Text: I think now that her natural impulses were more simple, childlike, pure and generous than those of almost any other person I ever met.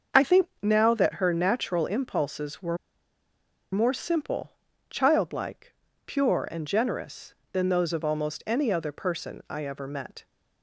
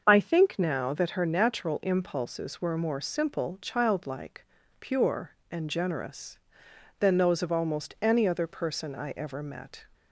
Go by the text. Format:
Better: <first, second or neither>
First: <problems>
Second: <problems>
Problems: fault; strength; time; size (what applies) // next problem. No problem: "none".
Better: second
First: starts louder than the rest; until 1.3 s; 6.5 dB // pauses between "think" and "now"; slight; at 0.4 s; 0.16 s long // pauses between "were" and "more"; noticeable; at 2.7 s; 0.97 s long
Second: starts louder than the rest; until 1.0 s; 6.5 dB